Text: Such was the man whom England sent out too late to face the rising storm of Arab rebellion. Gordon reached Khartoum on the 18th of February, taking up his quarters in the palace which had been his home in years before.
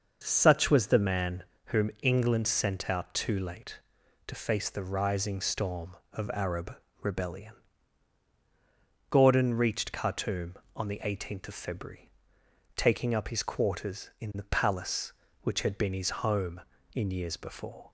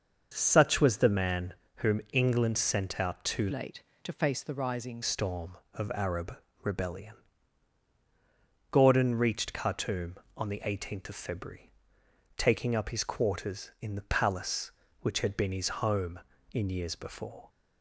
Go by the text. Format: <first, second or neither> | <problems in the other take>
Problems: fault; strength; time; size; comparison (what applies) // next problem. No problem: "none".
first | starts louder than the rest; until 1.3 s; 6.5 dB; also in the first // pauses between "man" and "whom"; slight; at 1.5 s; 0.24 s long; slight in the first // changes voice from "late" to "rising"; from 3.5 to 5.0 s; 1.5 s long // pauses between "Arab" and "rebellion"; slight; at 6.3 s; 0.26 s long; slight in the first